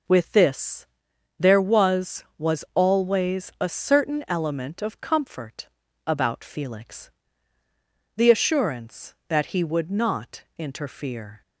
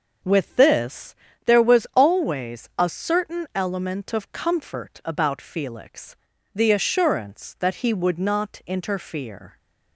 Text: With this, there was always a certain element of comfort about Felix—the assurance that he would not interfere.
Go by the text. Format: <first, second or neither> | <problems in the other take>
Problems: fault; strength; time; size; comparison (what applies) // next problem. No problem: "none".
second | says "was" twice; at 2.3 s // pauses between "comfort" and "about"; at 5.6 s; 0.38 s long